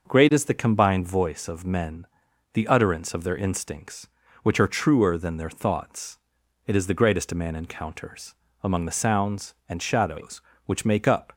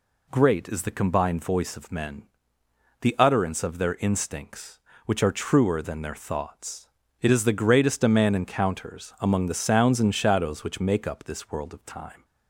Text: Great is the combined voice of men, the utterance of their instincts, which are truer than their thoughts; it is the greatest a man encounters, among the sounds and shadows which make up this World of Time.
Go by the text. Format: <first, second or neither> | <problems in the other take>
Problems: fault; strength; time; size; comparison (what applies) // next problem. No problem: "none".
second | starts louder than the rest; noticeable; until 1.1 s; 6 dB // stops before "this World of Time"; at 11.3 s